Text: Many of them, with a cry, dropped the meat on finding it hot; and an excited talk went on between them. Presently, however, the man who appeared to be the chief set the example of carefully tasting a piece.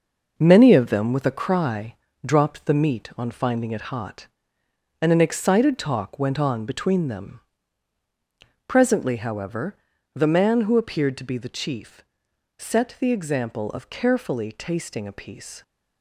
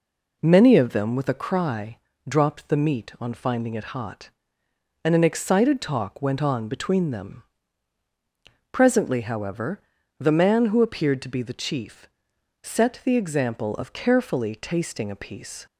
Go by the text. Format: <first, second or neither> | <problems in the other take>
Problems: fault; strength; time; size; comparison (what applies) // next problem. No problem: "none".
second | gets quieter; strong; throughout; 8 dB // pauses between "chief" and "set"; noticeable; at 12.0 s; 0.56 s long; noticeable in the second